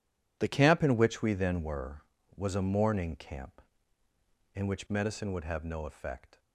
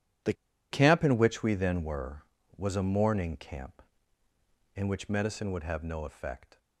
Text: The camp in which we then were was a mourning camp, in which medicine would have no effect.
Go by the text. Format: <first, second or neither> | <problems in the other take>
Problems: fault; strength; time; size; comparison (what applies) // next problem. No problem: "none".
first | pauses between "The" and "camp"; at 0.3 s; 0.38 s long